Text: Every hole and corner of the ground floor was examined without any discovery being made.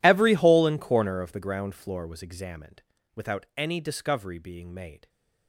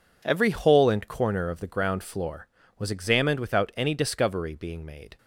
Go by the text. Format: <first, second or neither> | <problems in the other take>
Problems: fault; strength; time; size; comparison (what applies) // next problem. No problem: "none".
second | gets quieter; strong; throughout; 22 dB // pauses between "examined" and "without"; slight; at 2.8 s; 0.34 s long